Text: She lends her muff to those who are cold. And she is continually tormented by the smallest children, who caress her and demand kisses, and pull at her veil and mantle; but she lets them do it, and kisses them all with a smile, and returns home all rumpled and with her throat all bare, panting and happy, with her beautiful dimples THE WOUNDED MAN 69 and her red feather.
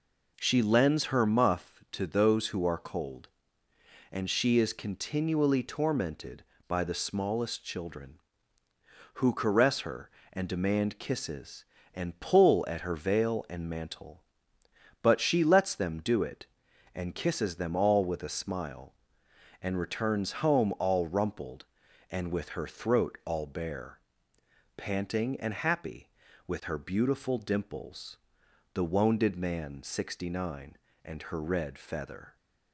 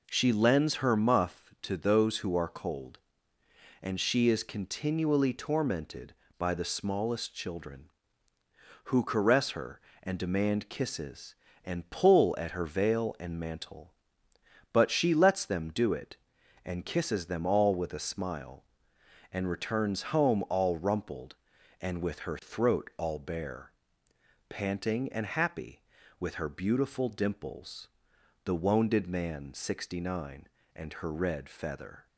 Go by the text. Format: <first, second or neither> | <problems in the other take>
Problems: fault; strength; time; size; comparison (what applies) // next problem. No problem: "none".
neither | pauses between "dimples" and "THE"; noticeable; the same in both